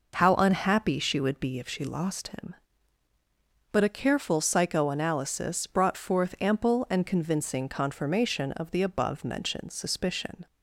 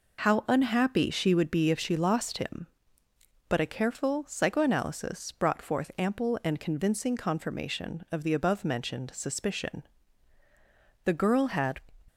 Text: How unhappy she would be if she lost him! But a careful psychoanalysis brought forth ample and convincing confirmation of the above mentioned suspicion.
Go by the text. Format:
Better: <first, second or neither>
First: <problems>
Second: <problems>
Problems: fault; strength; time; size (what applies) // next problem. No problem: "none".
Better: first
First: none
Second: goes on to say "The girl had"; noticeable; from 11.0 s on; 0.74 s long